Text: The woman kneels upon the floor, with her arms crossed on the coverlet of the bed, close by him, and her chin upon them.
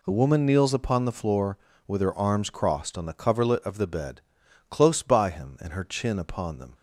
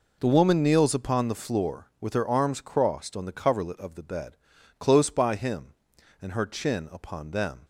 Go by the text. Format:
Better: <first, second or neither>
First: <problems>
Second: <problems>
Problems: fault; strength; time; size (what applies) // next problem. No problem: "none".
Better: neither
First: none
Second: none